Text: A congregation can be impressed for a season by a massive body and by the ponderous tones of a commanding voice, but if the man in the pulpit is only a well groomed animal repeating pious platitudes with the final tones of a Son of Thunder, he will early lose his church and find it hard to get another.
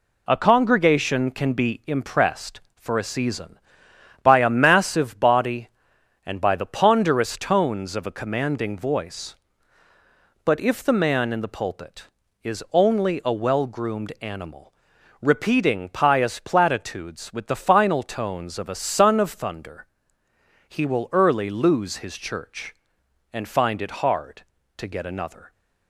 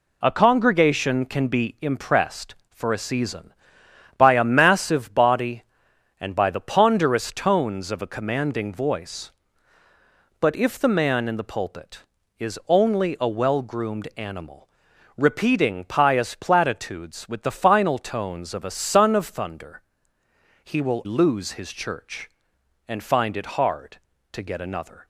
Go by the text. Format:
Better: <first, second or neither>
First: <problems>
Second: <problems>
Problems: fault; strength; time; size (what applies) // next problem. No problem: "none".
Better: first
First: pauses between "animal" and "repeating"; noticeable; at 14.7 s; 0.48 s long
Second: pauses between "animal" and "repeating"; noticeable; at 14.6 s; 0.48 s long // skips "early"; at 21.0 s